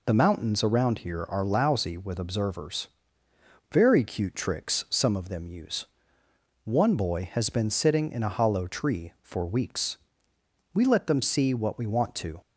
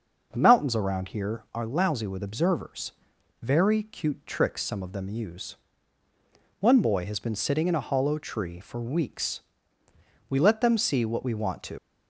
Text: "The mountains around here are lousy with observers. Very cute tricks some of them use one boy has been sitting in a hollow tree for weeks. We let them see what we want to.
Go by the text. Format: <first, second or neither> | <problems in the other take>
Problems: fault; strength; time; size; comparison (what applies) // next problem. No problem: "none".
first | starts louder than the rest; noticeable; until 1.3 s; 6 dB // pauses between "use" and "one"; at 5.5 s; 1.0 s long; noticeable in the first // leaves "to" unfinished; at 11.7 s; 75 ms